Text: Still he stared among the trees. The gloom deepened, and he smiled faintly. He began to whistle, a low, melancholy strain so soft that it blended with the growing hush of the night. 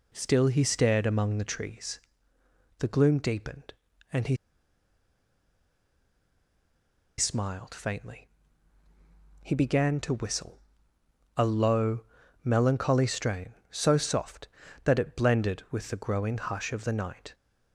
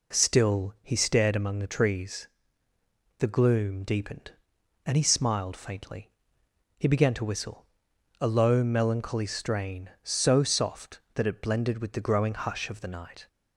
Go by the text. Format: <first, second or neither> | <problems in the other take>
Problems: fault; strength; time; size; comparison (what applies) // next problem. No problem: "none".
second | pauses between "he" and "smiled"; strong; at 4.3 s; 2.8 s long